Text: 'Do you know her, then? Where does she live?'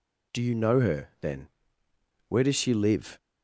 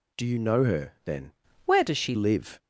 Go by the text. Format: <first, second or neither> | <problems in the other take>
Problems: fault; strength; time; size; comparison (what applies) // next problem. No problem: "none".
first | changes voice from "Where" to "she"; from 1.6 to 2.1 s; 0.5 s long